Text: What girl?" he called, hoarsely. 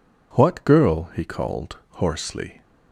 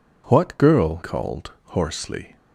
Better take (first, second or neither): first